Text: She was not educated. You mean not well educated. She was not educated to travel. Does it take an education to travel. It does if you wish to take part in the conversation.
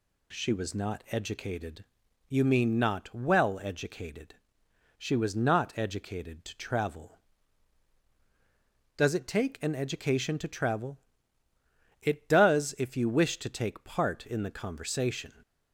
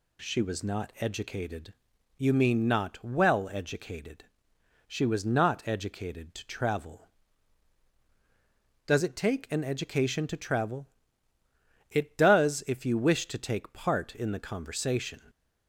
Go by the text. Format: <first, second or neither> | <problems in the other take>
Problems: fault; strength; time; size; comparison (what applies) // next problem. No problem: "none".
neither | none